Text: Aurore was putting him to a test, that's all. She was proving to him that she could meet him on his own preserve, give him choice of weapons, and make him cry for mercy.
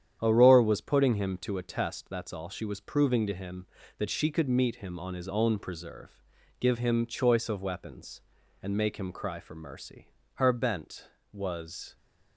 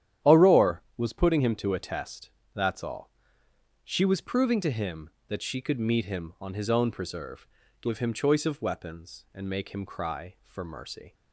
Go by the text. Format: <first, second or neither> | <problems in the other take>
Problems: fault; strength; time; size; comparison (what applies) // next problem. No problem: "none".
second | starts louder than the rest; strong; until 1.2 s; 9.5 dB; strong in the second // goes on to say "Her bent was"; from 10.3 s on; 1.6 s long